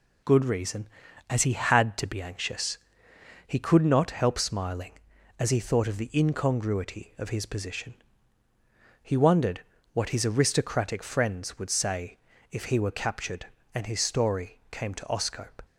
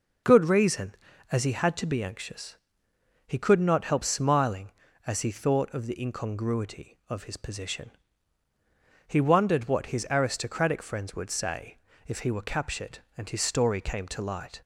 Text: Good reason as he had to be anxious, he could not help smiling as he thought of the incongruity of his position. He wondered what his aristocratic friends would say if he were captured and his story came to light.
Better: second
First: pauses between "wondered" and "what"; slight; at 9.6 s; 0.32 s long // pauses between "say" and "if"; slight; at 12.1 s; 0.34 s long // says "oscope" for "light"; at 15.0 s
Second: pauses between "say" and "if"; slight; at 11.7 s; 0.28 s long

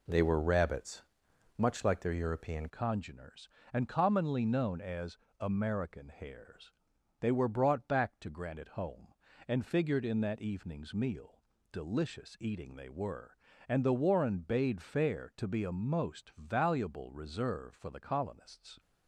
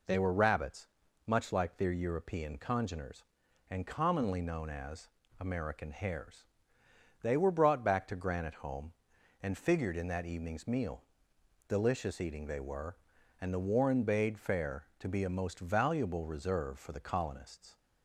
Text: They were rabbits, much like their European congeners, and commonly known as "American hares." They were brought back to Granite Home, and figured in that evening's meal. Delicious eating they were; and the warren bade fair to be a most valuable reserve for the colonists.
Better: second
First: changes voice at "congeners"; from 2.6 s on; 16.1 s long // pauses between "as" and "American"; slight; at 5.1 s; 0.24 s long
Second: pauses between "as" and "American"; slight; at 5.0 s; 0.32 s long

